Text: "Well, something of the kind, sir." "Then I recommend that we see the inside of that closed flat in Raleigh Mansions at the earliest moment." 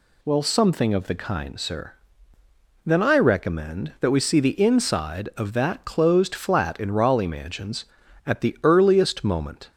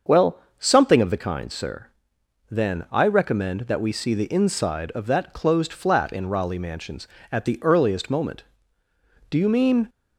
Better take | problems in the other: first | starts louder than the rest; until 1.2 s; 6.5 dB // goes on to say "Do you mean"; from 9.2 s on; 0.60 s long

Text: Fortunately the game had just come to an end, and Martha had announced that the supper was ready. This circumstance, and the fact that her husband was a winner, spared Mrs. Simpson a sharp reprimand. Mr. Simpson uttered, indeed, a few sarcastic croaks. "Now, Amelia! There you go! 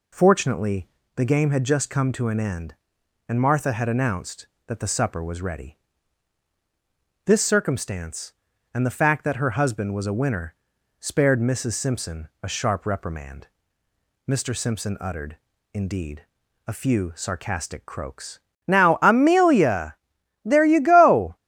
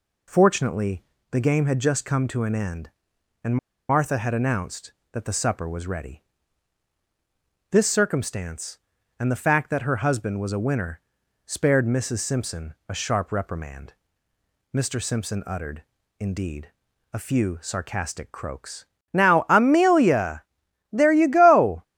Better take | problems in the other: first | pauses between "Fortunately" and "the"; slight; at 1.0 s; 0.30 s long; slight in the first // pauses between "and" and "Martha"; slight; at 3.5 s; 0.32 s long

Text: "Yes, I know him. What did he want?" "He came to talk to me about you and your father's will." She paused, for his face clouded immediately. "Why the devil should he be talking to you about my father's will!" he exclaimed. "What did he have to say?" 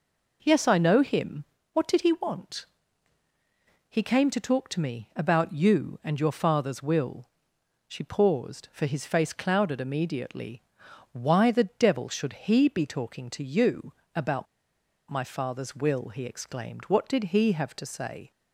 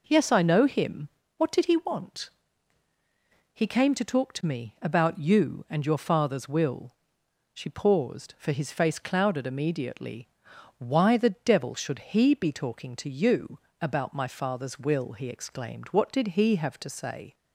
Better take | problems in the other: second | pauses between "you" and "about"; slight; at 13.9 s; 0.24 s long; slight in the second // pauses between "about" and "my"; noticeable; at 14.4 s; 0.64 s long

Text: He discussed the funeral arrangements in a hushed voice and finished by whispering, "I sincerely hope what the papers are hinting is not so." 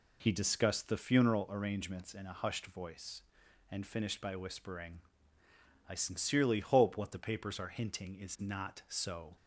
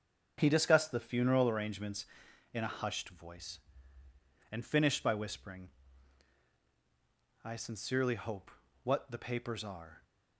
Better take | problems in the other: first | starts louder than the rest; until 1.3 s; 7 dB // pauses between "hope" and "what"; slight; at 8.4 s; 0.32 s long // stops before "hinting is not so"; at 10.0 s

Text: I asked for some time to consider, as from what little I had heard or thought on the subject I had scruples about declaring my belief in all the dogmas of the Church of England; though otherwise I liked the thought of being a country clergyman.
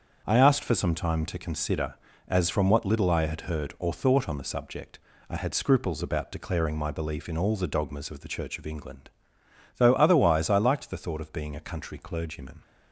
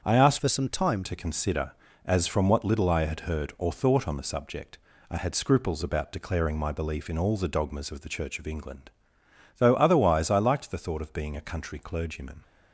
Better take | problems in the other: first | starts louder than the rest; strong; until 1.0 s; 7.5 dB; also in the first // changes voice from "for" to "time"; from 0.3 to 1.0 s; 0.7 s long // pauses between "subject" and "I"; slight; at 4.7 s; 0.32 s long; slight in the first

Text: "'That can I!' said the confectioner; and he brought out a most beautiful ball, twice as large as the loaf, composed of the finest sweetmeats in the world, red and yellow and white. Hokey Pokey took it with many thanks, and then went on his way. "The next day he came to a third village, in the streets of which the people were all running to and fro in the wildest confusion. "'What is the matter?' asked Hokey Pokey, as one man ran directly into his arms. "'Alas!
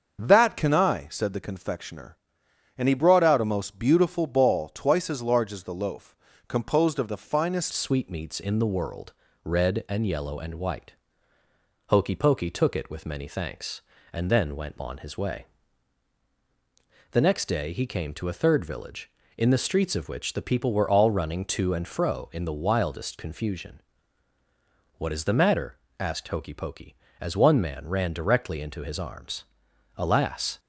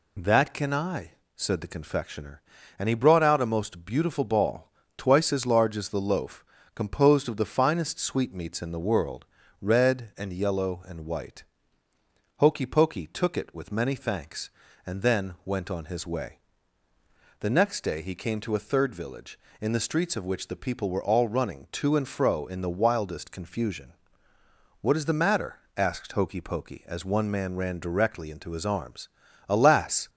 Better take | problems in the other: second | starts louder than the rest; until 1.2 s; 6.5 dB // changes voice at "sweetmeats"; from 7.7 s on; 22.8 s long

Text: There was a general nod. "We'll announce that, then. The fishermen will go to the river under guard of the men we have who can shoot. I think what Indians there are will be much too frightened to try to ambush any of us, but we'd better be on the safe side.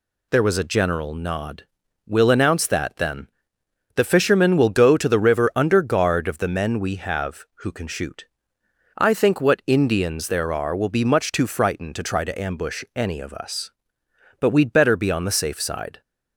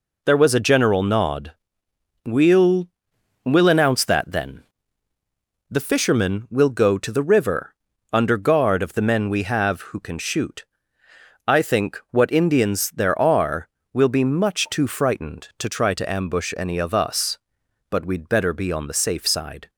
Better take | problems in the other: first | says "We'll" twice; at 3.4 s // pauses between "river" and "under"; at 7.7 s; 0.40 s long

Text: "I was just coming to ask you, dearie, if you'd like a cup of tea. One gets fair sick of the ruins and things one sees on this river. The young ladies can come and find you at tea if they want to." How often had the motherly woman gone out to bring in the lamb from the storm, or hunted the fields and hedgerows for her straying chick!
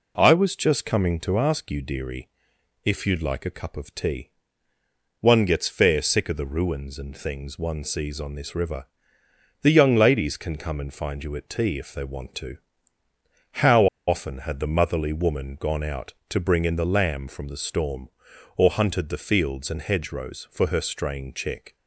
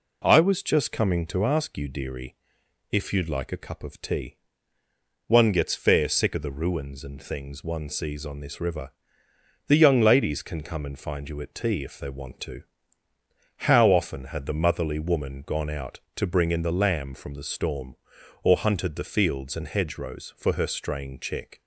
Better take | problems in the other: second | pauses between "How" and "often"; slight; at 13.8 s; 0.21 s long

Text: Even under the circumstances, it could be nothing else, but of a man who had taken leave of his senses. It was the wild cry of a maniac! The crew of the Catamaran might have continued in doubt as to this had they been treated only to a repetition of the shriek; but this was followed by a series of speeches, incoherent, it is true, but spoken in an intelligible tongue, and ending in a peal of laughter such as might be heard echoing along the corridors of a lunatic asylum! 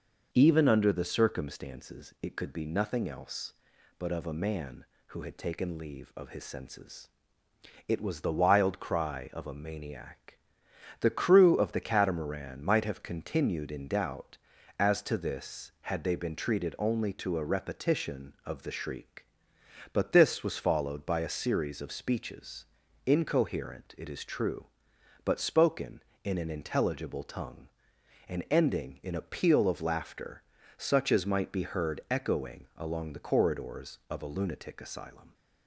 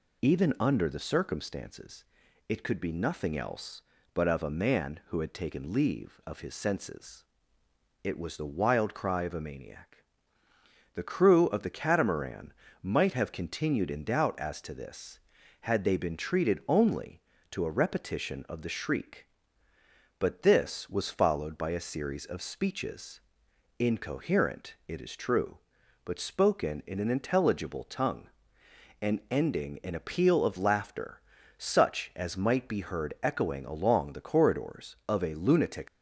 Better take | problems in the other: first | pauses between "Catamaran" and "might"; slight; at 12.5 s; 0.30 s long // pauses between "laughter" and "such"; at 31.2 s; 0.38 s long; slight in the first // stops before "asylum"; at 35.8 s

